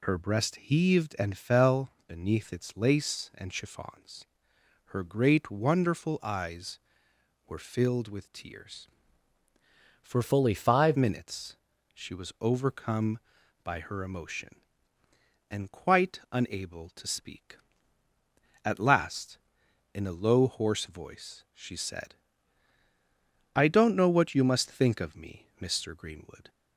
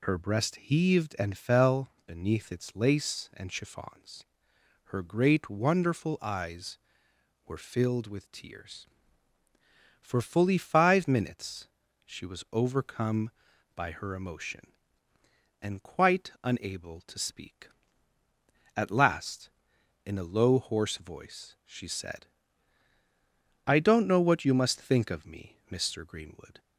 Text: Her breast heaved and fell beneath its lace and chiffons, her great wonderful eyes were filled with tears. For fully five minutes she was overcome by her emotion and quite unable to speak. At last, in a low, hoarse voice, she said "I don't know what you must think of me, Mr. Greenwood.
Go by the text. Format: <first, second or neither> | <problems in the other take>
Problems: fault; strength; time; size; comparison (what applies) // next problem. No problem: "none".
second | changes voice from "fully" to "five"; from 10.2 to 10.9 s; 0.7 s long // pauses between "minutes" and "she"; slight; at 11.5 s; 0.36 s long; slight in the second // pauses between "said" and "I"; strong; at 22.1 s; 1.4 s long; strong in the second